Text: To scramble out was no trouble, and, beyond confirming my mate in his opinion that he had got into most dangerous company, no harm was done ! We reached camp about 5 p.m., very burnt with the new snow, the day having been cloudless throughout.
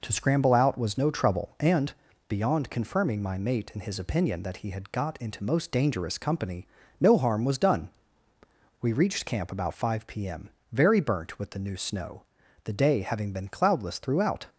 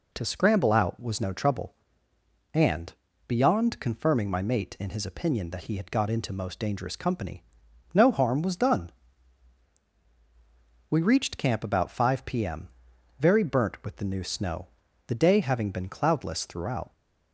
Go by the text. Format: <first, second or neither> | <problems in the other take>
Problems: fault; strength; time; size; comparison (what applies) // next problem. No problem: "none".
neither | none